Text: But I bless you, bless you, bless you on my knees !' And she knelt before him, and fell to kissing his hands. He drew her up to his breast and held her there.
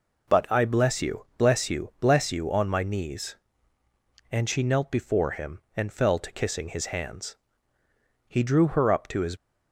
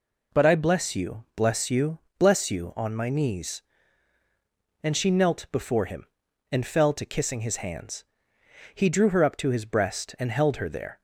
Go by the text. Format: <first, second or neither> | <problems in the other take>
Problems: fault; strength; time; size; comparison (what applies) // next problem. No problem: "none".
second | stops before "breast and held her there"; at 9.3 s